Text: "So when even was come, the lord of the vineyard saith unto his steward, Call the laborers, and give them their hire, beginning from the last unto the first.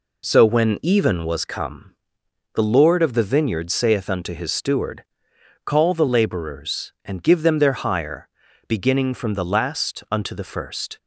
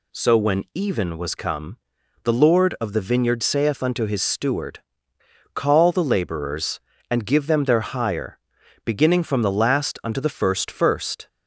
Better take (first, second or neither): first